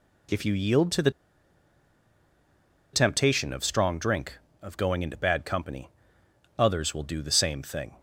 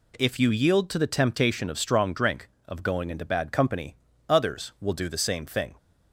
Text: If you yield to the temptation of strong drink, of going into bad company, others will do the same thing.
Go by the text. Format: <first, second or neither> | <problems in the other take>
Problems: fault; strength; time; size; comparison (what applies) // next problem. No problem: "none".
second | pauses between "the" and "temptation"; strong; at 1.0 s; 1.8 s long